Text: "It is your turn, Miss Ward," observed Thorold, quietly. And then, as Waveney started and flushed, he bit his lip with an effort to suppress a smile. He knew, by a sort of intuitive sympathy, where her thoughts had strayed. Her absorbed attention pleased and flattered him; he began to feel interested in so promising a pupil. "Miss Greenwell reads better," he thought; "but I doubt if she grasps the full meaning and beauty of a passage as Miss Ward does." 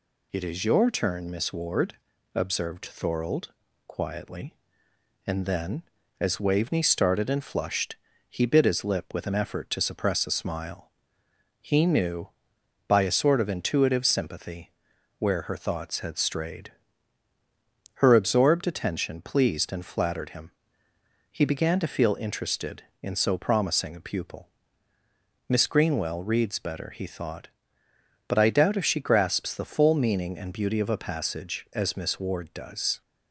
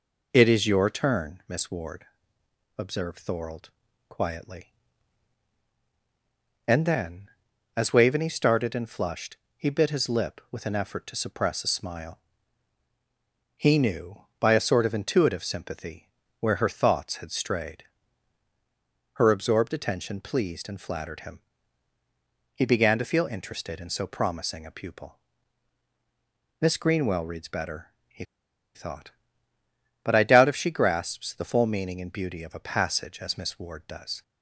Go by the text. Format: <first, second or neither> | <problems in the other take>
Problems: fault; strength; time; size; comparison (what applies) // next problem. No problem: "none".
first | pauses between "he" and "thought"; noticeable; at 28.2 s; 0.50 s long